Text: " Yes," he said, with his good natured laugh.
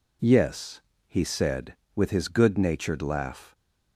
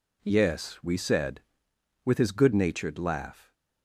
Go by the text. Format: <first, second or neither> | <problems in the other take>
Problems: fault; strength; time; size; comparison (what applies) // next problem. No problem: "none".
first | says "we" for "he"; at 0.8 s